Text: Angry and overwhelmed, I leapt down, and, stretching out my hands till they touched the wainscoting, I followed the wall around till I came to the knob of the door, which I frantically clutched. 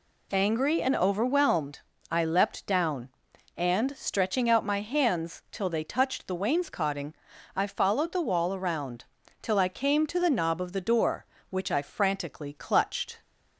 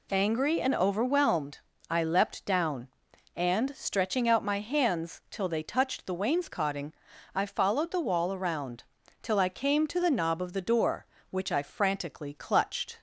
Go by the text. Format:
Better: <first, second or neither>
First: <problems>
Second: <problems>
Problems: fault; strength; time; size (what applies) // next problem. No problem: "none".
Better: neither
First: pauses between "around" and "till"; at 9.0 s; 0.36 s long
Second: pauses between "around" and "till"; at 8.8 s; 0.38 s long